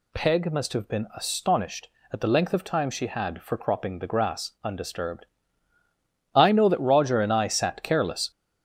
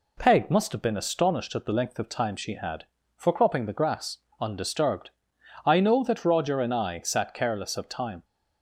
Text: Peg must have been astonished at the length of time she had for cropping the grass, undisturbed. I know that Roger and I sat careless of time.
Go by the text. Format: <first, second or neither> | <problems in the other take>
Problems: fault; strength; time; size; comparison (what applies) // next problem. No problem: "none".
second | stops before "of time"; at 8.3 s